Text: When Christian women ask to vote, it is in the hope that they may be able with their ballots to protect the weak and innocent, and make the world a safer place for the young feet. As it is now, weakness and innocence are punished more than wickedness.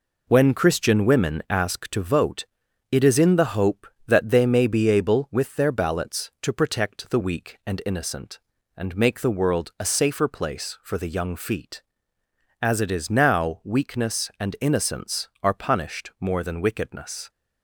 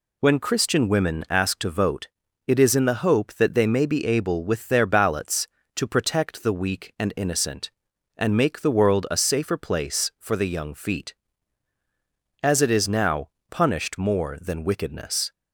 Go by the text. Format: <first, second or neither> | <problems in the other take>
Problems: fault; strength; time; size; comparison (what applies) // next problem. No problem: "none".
first | skips "weakness and innocence are"; at 13.3 s